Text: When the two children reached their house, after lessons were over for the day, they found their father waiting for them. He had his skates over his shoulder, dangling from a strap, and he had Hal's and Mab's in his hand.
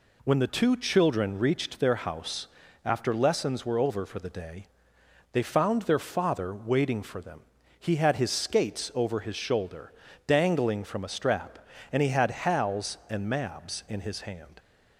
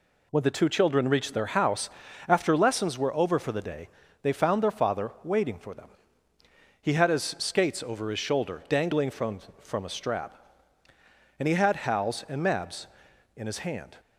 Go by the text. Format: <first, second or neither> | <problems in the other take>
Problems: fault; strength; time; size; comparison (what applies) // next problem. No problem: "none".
first | says "from" twice; at 9.5 s